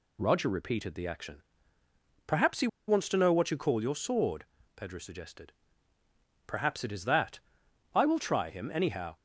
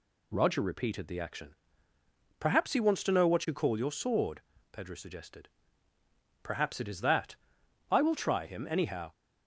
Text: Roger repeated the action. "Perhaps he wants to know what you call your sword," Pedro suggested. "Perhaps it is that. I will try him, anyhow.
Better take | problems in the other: second | pauses between "he" and "wants"; slight; at 2.6 s; 0.20 s long

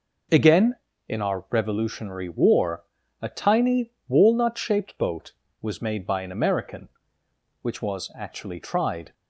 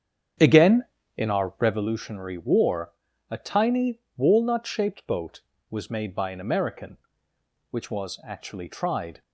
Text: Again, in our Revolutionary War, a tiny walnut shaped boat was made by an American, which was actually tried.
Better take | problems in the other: first | starts louder than the rest; strong; until 2.0 s; 8 dB // pauses between "tiny" and "walnut"; slight; at 3.9 s; 0.18 s long; slight in the first

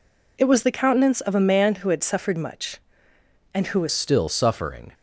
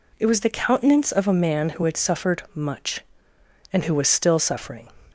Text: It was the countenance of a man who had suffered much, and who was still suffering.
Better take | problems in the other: second | changes voice at "still"; from 3.9 s on; 1.0 s long

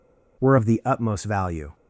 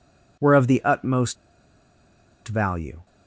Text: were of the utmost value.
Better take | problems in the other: first | pauses between "utmost" and "value"; at 1.3 s; 1.1 s long

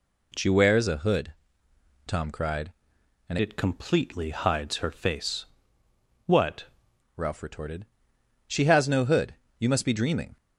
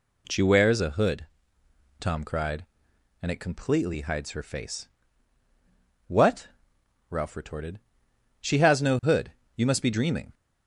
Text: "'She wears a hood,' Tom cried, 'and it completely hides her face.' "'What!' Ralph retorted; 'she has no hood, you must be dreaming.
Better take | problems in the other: second | changes voice from "it" to "What"; from 3.3 to 6.6 s; 3.3 s long

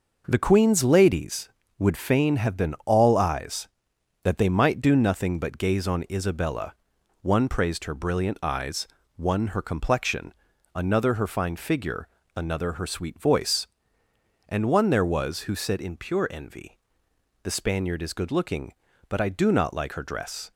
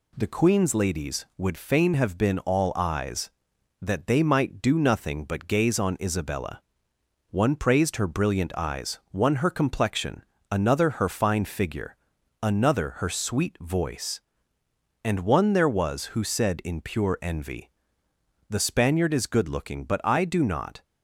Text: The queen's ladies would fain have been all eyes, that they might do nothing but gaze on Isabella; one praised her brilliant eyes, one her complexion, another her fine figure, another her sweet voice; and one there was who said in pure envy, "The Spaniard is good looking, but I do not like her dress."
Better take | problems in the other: first | stops before "like her dress"; at 20.8 s

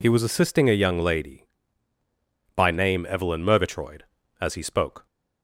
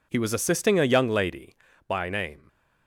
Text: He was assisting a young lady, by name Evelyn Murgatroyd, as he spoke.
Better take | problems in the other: first | stops before "Evelyn Murgatroyd as he spoke"; at 2.4 s

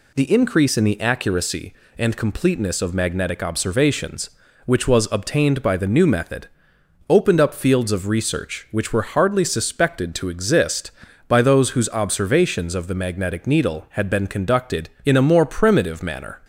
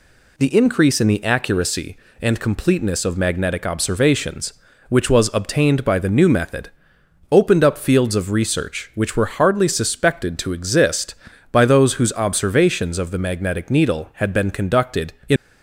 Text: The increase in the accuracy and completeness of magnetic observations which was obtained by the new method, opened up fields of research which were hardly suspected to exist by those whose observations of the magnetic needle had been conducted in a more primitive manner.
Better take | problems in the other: first | stops before "a more primitive manner"; at 15.3 s

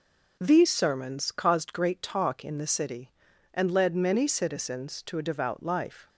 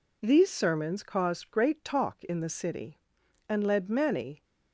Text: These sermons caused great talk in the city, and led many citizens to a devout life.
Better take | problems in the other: first | stops before "citizens to a devout life"; at 4.4 s

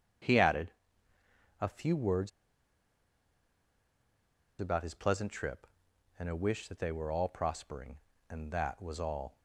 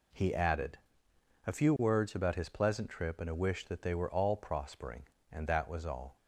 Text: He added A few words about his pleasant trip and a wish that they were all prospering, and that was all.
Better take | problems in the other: second | starts louder than the rest; strong; until 2.1 s; 7.5 dB // pauses between "added" and "A"; noticeable; at 0.6 s; 0.90 s long; noticeable in the second // pauses between "words" and "about"; strong; at 2.3 s; 2.2 s long

